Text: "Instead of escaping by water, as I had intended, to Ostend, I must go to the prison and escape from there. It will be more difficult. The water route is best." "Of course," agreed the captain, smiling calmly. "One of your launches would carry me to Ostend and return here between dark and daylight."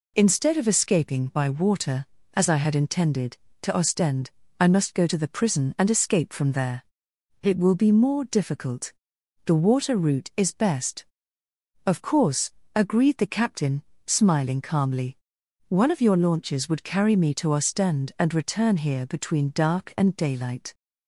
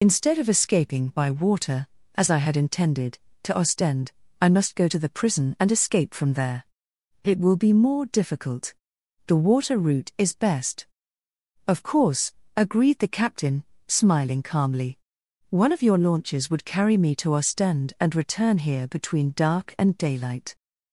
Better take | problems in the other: first | loses the start of "Instead"; at 0.0 s; 45 ms

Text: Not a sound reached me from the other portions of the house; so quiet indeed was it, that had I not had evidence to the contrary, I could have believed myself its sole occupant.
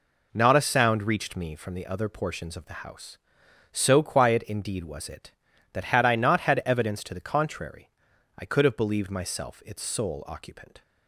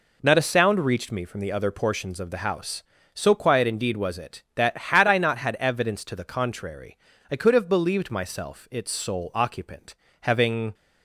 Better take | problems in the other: first | goes on to say "Having"; from 10.2 s on; 0.50 s long

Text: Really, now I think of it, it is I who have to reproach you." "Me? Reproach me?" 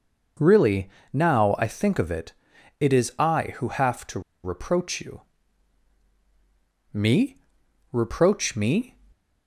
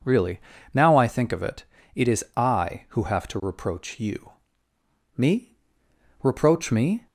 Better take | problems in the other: second | pauses between "to" and "reproach"; slight; at 4.1 s; 0.23 s long

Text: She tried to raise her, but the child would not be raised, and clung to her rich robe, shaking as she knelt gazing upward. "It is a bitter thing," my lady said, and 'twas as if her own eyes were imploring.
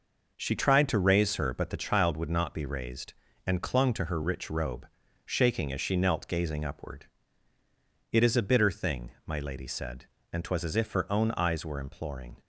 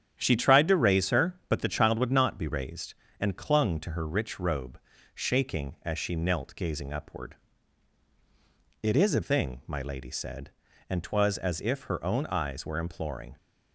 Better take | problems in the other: first | starts louder than the rest; strong; until 1.2 s; 9.5 dB // skips "bitter"; at 9.2 s

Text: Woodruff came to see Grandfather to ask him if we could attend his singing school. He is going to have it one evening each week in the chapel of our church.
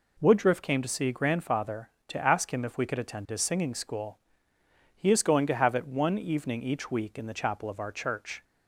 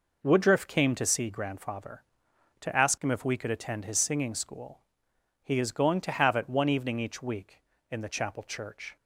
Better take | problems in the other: first | skips "of our"; at 8.4 s

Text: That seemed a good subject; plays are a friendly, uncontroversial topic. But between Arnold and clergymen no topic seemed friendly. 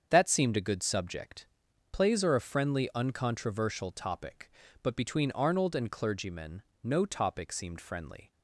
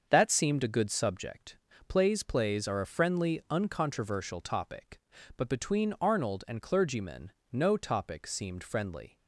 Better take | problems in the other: first | starts louder than the rest; until 1.1 s; 6.5 dB; strong in the first // says "plays" twice; at 2.2 s // pauses between "clergymen" and "no"; slight; at 7.3 s; 0.20 s long; slight in the first

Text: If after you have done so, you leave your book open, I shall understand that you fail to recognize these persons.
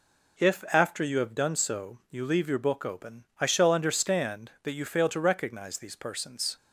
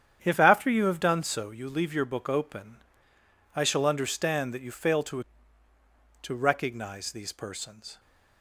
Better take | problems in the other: first | starts louder than the rest; strong; until 1.2 s; 9 dB // says "to" twice; at 6.2 s

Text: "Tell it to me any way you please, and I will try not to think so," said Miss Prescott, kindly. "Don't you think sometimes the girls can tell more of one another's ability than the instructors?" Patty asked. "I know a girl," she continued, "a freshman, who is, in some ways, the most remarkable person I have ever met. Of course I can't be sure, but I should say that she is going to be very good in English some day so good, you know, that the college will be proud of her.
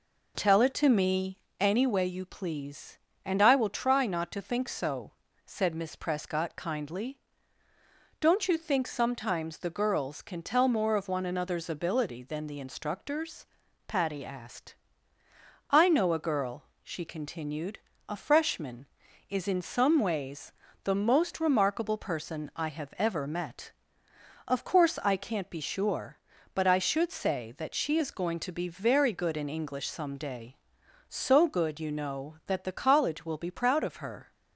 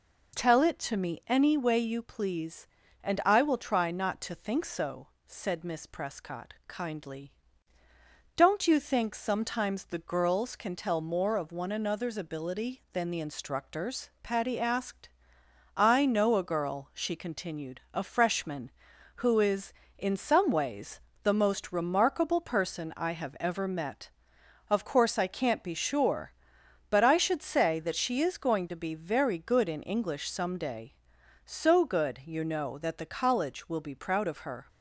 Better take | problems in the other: second | pauses between "me" and "any"; slight; at 1.3 s; 0.20 s long // skips "who"; at 19.0 s

